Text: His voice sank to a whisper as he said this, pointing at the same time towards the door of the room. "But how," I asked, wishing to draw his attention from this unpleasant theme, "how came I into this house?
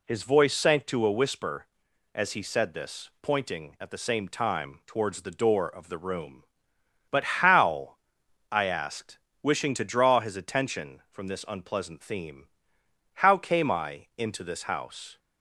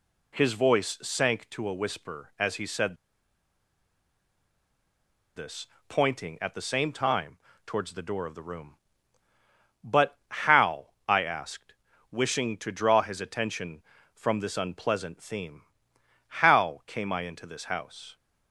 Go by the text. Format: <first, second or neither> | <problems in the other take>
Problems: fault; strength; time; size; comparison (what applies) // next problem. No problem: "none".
first | pauses between "said" and "this"; strong; at 2.9 s; 2.4 s long // pauses between "time" and "towards"; slight; at 7.3 s; 0.30 s long